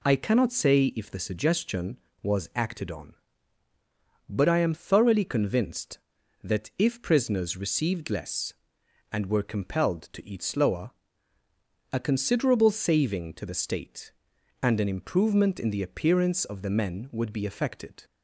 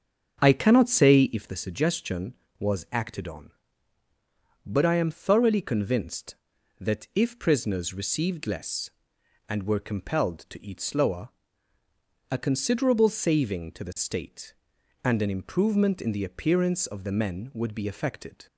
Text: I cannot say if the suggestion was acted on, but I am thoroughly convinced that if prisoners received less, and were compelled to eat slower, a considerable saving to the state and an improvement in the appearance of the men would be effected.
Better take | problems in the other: first | starts louder than the rest; strong; until 1.5 s; 7.5 dB

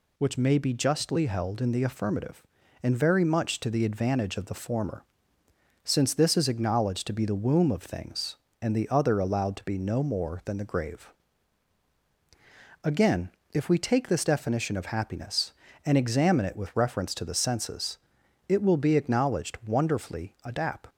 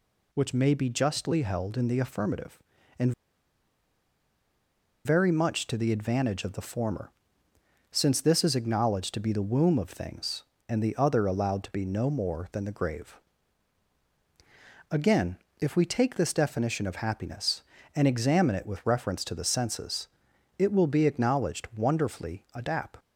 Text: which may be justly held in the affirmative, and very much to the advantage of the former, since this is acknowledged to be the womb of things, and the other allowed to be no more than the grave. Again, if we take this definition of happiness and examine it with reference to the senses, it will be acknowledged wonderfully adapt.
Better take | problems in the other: first | pauses between "and" and "very"; strong; at 3.1 s; 1.9 s long

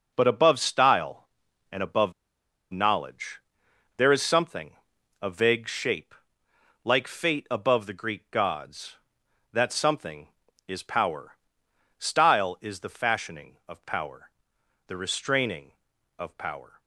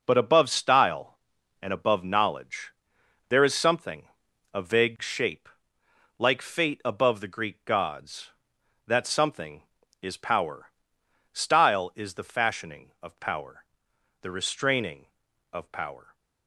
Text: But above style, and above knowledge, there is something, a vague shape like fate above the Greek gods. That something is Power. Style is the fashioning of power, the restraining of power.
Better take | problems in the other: second | pauses between "above" and "knowledge"; noticeable; at 2.1 s; 0.58 s long // pauses between "shape" and "like"; noticeable; at 6.1 s; 0.68 s long; noticeable in the second

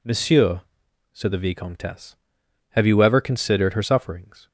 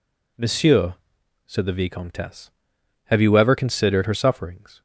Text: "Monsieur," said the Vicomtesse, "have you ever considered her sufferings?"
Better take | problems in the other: neither | none

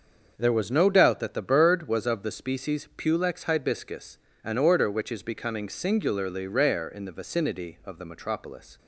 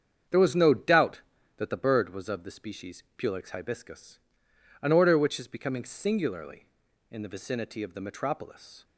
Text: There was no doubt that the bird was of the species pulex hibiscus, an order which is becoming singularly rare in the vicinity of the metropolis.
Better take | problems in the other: first | starts louder than the rest; strong; until 1.6 s; 7.5 dB; also in the first // pauses between "species" and "pulex"; slight; at 3.0 s; 0.16 s long // skips "rare"; at 6.8 s

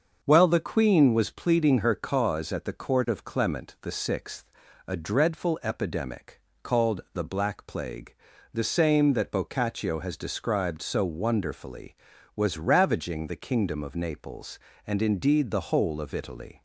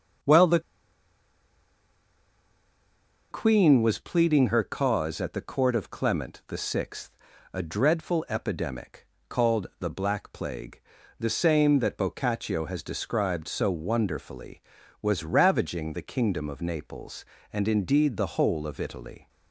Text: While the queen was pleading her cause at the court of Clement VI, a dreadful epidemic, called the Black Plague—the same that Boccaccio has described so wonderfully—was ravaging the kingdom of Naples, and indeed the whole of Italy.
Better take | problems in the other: first | starts louder than the rest; until 3.9 s; 6.5 dB; also in the first // pauses between "the" and "queen"; strong; at 0.5 s; 2.7 s long

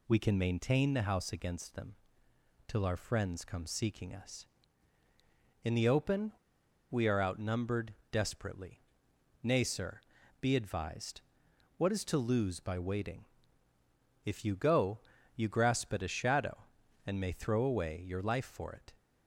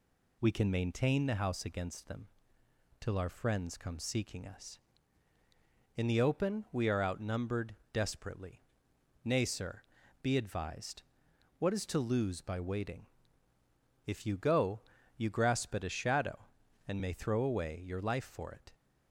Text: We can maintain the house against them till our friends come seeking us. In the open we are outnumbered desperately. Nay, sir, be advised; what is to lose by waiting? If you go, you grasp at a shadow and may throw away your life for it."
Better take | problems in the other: second | pauses between "them" and "till"; noticeable; at 1.9 s; 0.72 s long; noticeable in the second // pauses between "open" and "we"; noticeable; at 6.3 s; 0.58 s long // pauses between "outnumbered" and "desperately"; slight; at 7.9 s; 0.18 s long; slight in the second

